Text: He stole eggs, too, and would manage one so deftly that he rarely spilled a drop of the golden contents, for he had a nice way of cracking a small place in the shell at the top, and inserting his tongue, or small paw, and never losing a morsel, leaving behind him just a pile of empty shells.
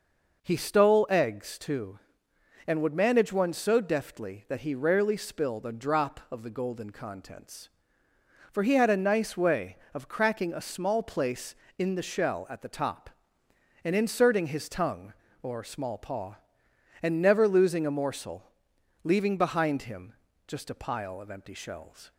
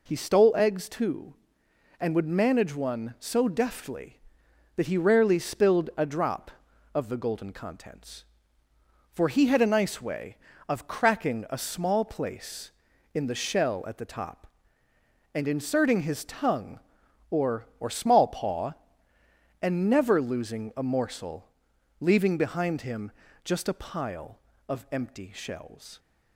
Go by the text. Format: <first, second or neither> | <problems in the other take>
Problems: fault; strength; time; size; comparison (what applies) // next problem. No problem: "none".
first | says "or" twice; at 17.8 s // pauses between "him" and "just"; slight; at 23.1 s; 0.32 s long; slight in the first